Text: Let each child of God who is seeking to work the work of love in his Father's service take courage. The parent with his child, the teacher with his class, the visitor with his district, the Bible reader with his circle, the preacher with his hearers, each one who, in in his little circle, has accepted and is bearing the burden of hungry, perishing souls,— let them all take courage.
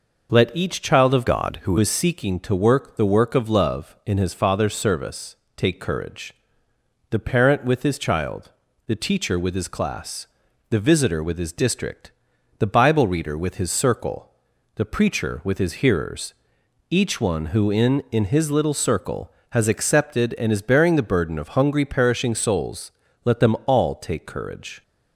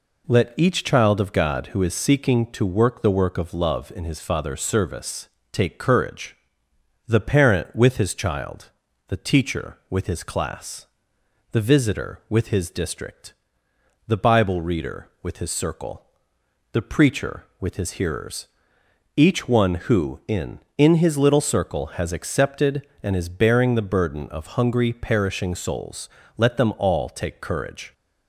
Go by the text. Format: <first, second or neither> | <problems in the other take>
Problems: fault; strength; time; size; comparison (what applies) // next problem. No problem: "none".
second | changes voice from "God" to "who"; from 1.2 to 1.7 s; 0.5 s long // pauses between "service" and "take"; slight; at 5.3 s; 0.20 s long; slight in the second